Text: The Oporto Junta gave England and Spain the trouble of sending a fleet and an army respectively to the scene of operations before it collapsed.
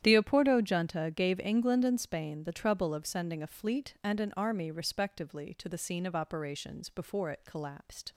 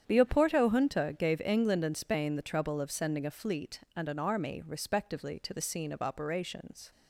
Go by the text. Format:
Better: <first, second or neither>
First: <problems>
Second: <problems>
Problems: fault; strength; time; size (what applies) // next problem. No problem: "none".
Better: first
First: starts louder than the rest; strong; until 1.0 s; 10.5 dB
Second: starts louder than the rest; strong; until 1.0 s; 9 dB // stops before "before it collapsed"; at 6.9 s